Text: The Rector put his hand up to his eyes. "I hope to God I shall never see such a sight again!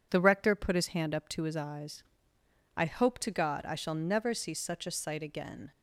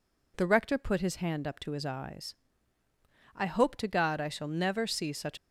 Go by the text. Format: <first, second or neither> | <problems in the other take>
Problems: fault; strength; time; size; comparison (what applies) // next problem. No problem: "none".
first | stops before "a sight again"; at 5.3 s